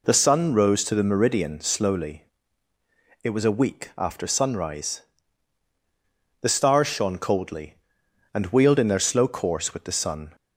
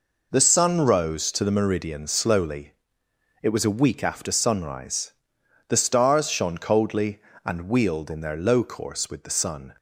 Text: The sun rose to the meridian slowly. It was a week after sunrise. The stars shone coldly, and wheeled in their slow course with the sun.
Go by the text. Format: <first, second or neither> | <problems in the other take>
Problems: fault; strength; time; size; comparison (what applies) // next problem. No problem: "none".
first | says "low" for "slow"; at 8.3 s